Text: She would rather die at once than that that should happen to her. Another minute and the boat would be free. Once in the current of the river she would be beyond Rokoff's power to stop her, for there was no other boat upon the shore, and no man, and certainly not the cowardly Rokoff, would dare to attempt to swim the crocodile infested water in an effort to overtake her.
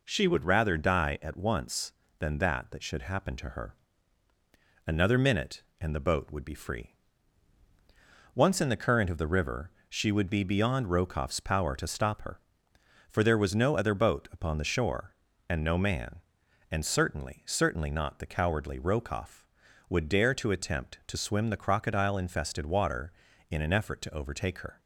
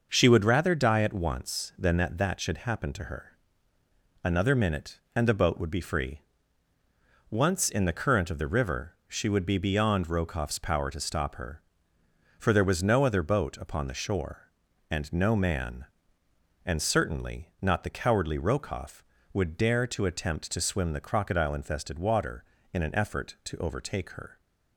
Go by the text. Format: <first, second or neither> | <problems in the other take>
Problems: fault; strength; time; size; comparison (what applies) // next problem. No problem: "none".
second | pauses between "river" and "she"; slight; at 9.7 s; 0.18 s long // says "certainly" twice; at 17.4 s